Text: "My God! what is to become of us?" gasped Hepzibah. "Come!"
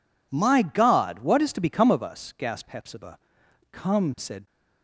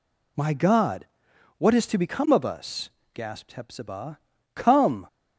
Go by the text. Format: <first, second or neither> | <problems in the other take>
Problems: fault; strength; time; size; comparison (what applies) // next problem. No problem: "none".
second | goes on to say "said"; slight; from 4.1 s on; 0.28 s long